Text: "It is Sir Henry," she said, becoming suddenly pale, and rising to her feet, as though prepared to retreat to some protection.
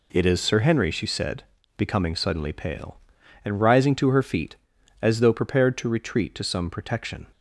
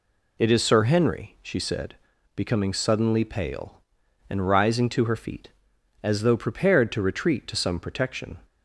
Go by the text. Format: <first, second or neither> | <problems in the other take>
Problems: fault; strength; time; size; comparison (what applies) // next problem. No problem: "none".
neither | none